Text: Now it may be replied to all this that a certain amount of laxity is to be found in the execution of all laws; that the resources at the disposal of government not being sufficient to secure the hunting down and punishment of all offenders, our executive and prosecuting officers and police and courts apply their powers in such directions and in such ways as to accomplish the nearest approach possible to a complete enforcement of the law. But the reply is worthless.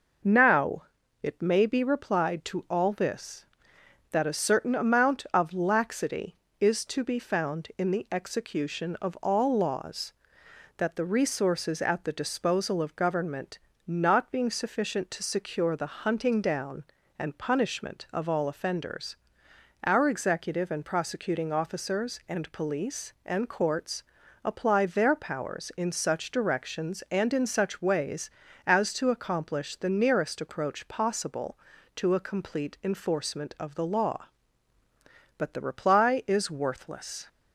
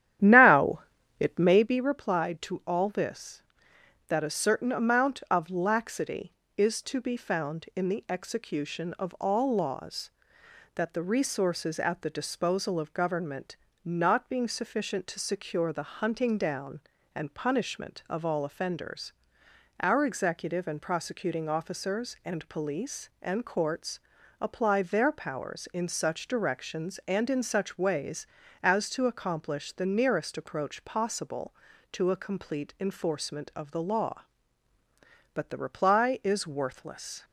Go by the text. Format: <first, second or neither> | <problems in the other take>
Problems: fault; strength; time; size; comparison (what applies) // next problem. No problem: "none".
first | starts louder than the rest; strong; until 1.7 s; 11 dB // pauses between "Now" and "it"; at 0.8 s; 0.38 s long; also in the first // pauses between "government" and "not"; slight; at 13.5 s; 0.26 s long; slight in the first // pauses between "courts" and "apply"; at 23.9 s; 0.42 s long; also in the first